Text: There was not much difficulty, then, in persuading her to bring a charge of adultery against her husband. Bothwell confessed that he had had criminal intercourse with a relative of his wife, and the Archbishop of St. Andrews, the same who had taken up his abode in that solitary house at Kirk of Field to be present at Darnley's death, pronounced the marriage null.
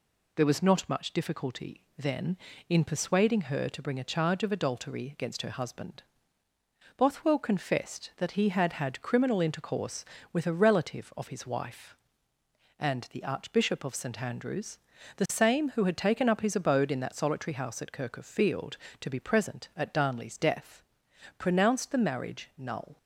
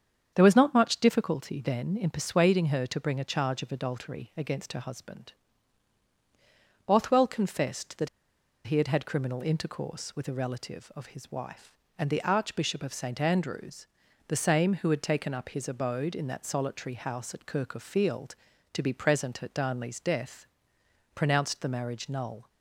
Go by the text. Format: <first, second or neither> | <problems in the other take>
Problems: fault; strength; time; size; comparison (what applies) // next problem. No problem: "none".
first | starts louder than the rest; strong; until 1.3 s; 7.5 dB // pauses between "that" and "he"; noticeable; at 8.0 s; 0.58 s long